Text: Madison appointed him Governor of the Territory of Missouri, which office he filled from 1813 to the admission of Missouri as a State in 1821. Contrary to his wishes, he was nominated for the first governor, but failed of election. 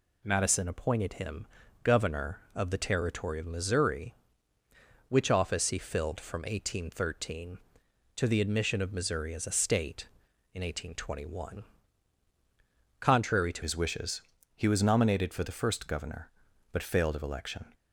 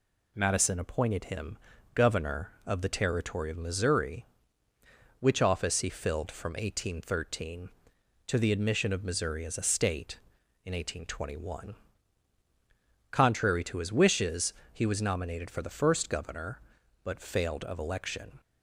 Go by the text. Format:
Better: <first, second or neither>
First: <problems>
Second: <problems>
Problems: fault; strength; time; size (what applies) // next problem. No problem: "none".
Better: second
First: pauses between "him" and "Governor"; at 1.4 s; 0.38 s long // changes voice at "his"; from 13.6 s on; 4.1 s long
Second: pauses between "him" and "Governor"; at 1.5 s; 0.38 s long